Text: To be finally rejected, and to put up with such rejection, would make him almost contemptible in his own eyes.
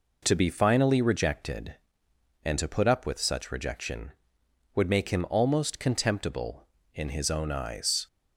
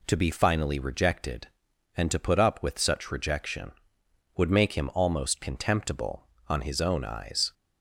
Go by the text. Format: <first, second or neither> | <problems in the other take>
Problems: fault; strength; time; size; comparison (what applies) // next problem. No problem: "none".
first | says "on" for "in"; at 6.4 s